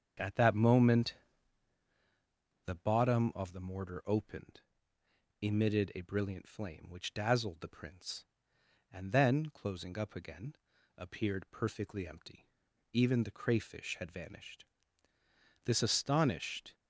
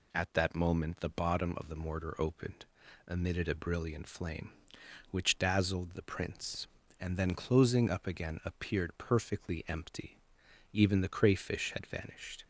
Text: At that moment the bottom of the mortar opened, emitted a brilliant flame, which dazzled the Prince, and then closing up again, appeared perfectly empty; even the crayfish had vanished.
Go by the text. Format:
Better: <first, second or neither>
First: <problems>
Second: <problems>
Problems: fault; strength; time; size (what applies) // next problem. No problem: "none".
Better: second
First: starts louder than the rest; until 2.7 s; 7 dB // pauses between "moment" and "the"; strong; at 1.1 s; 1.5 s long // goes on to say "This astonished"; noticeable; from 15.6 s on; 1.1 s long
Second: none